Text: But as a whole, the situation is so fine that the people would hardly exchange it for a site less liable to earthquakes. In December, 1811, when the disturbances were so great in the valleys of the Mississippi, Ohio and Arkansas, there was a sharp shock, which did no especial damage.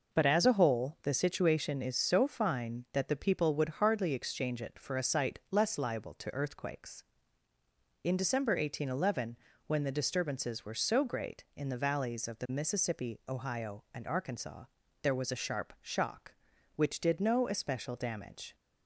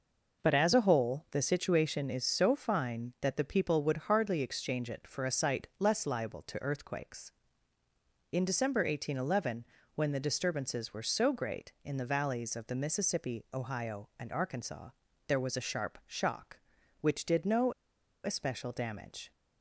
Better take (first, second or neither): first